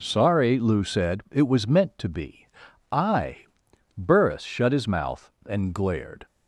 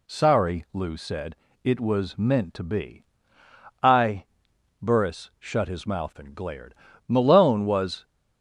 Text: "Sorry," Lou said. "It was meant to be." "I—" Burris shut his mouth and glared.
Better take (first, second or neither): first